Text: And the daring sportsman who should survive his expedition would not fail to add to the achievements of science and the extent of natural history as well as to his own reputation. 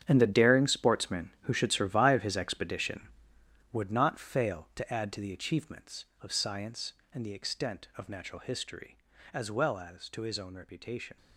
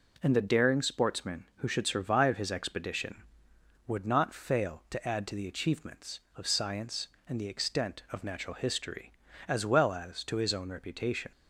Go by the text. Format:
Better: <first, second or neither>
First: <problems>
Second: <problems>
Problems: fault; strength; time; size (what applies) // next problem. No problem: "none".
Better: second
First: gets quieter; strong; throughout; 13.5 dB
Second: none